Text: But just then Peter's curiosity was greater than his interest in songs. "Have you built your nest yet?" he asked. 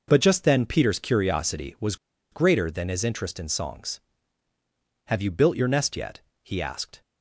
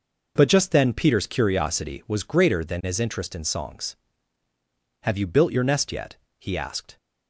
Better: second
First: pauses between "was" and "greater"; at 1.9 s; 0.36 s long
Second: none

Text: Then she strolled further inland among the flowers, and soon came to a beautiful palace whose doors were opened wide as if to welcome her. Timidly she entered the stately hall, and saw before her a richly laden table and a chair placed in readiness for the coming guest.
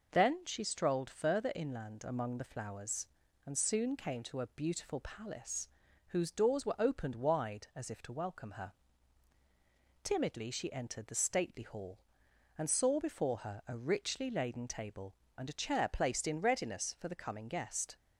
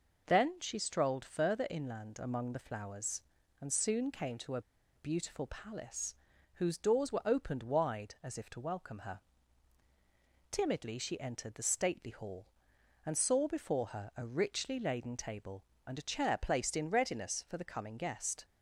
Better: first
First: pauses between "palace" and "whose"; at 5.6 s; 0.40 s long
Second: pauses between "a" and "beautiful"; slight; at 4.6 s; 0.34 s long // pauses between "palace" and "whose"; at 6.1 s; 0.40 s long

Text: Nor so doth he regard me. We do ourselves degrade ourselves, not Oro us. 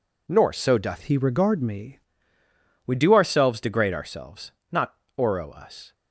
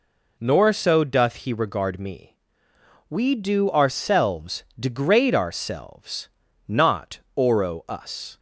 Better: second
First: changes voice from "he" to "me"; from 1.0 to 1.9 s; 0.9 s long // pauses between "not" and "Oro"; slight; at 4.9 s; 0.22 s long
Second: pauses between "not" and "Oro"; slight; at 7.2 s; 0.16 s long

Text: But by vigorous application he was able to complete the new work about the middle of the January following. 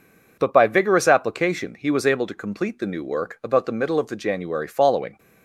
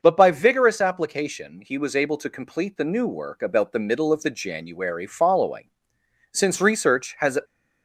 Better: first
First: none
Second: starts louder than the rest; until 1.0 s; 6 dB // goes on to say "Since research has"; noticeable; from 6.3 s on; 1.0 s long

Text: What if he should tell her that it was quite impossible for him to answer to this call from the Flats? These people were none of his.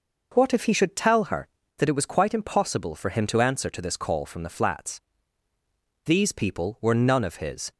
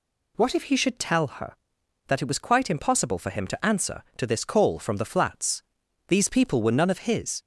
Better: neither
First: none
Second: none

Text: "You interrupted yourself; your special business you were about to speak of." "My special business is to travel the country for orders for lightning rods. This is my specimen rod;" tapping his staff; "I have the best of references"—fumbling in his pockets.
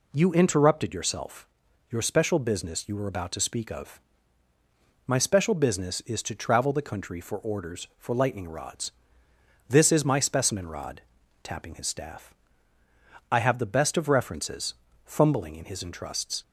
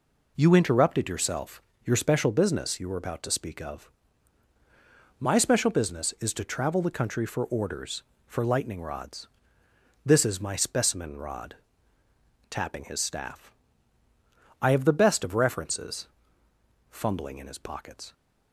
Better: second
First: says "entrusts" for "pockets"; at 15.8 s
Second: none

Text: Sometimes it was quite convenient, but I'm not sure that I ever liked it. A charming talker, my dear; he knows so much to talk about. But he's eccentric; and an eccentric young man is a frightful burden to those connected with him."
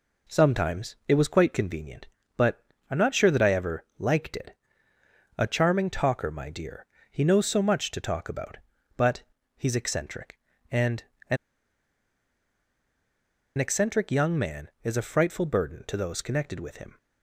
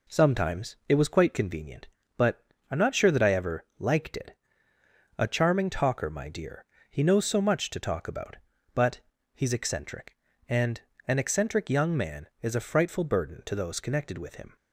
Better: second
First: pauses between "but" and "I'm"; slight; at 2.6 s; 0.28 s long // pauses between "But" and "he's"; slight; at 9.2 s; 0.34 s long // pauses between "and" and "an"; slight; at 11.0 s; 0.26 s long // pauses between "an" and "eccentric"; strong; at 11.3 s; 2.2 s long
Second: pauses between "but" and "I'm"; slight; at 2.4 s; 0.28 s long // pauses between "But" and "he's"; slight; at 8.9 s; 0.34 s long // pauses between "and" and "an"; slight; at 10.8 s; 0.26 s long

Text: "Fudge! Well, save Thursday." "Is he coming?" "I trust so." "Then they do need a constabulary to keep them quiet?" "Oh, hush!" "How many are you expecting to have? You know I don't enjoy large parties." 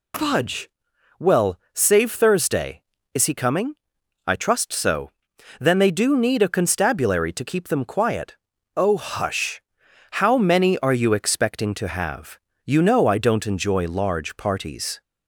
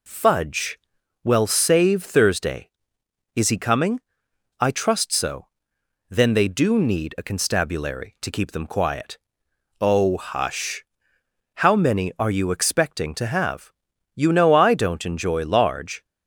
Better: first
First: none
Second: stops before "parties"; at 16.0 s

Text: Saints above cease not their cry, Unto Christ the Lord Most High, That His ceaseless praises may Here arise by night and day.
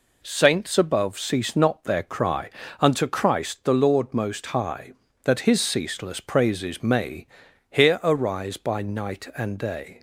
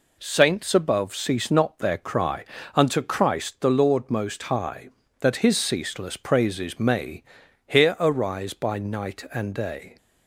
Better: neither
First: pauses between "may" and "Here"; noticeable; at 7.2 s; 0.46 s long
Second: pauses between "may" and "Here"; noticeable; at 7.2 s; 0.46 s long

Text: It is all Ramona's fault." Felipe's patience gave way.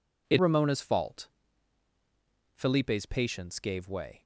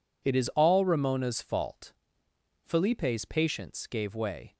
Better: second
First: skips "is all"; at 0.3 s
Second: none

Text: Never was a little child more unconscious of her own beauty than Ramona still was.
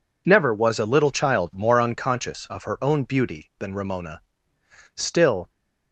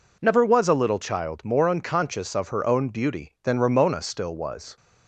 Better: second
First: pauses between "Ramona" and "still"; noticeable; at 4.2 s; 0.74 s long // stops before "was"; at 5.4 s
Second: none

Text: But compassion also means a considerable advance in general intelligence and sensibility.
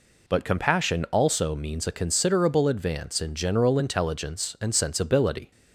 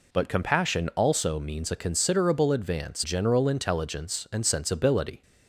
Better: first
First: none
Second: skips "in"; at 3.0 s

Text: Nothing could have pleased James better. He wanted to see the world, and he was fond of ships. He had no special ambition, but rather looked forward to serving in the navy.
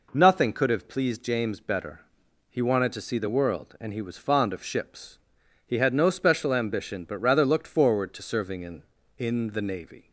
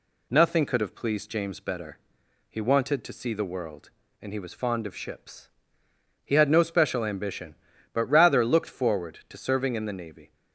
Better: second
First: says "in" twice; at 9.1 s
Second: none

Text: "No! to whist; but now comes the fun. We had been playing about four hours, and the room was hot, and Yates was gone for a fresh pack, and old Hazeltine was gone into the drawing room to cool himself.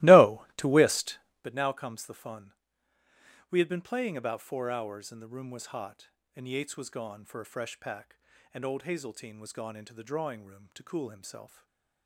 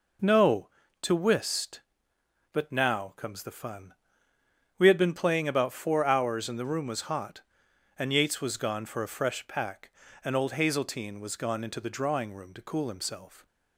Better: second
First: starts louder than the rest; strong; until 1.5 s; 18.5 dB // stays silent after the last word; slight; from 11.4 s on; 0.6 s long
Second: none

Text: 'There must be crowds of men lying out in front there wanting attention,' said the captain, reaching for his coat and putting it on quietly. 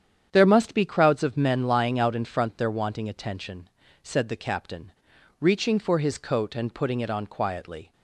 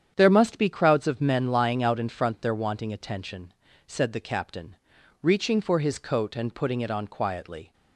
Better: neither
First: starts louder than the rest; strong; until 1.3 s; 8.5 dB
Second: starts louder than the rest; strong; until 1.1 s; 8.5 dB

